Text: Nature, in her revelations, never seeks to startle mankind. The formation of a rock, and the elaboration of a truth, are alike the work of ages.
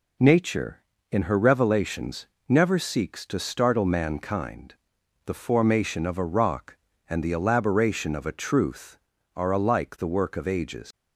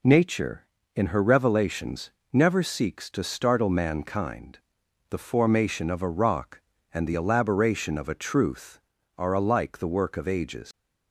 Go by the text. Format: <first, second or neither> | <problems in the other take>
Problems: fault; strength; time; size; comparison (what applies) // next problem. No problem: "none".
neither | none